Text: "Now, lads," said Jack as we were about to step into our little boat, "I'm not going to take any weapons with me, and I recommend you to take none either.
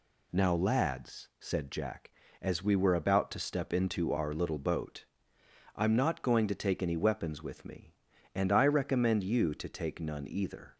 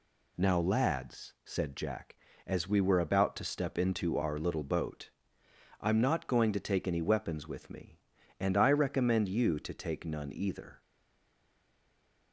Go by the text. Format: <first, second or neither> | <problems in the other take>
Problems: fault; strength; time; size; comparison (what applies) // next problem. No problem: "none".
first | stays silent after the last word; noticeable; from 10.8 s on; 1.5 s long